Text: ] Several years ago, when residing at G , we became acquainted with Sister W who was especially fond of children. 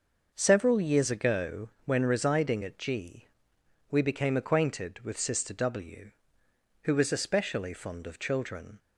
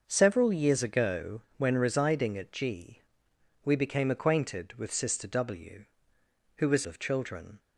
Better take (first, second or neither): first